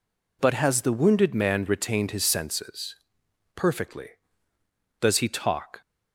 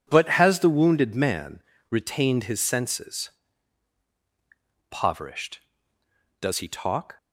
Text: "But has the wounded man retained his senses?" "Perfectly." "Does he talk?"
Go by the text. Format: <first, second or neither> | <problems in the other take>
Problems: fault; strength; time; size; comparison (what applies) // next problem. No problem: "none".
first | pauses between "man" and "retained"; slight; at 1.6 s; 0.28 s long // says "Poverished" for "Perfectly"; at 4.8 s